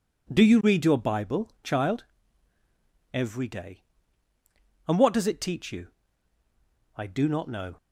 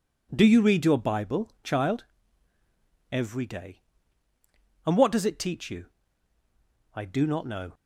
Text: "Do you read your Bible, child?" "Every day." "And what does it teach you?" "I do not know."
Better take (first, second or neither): neither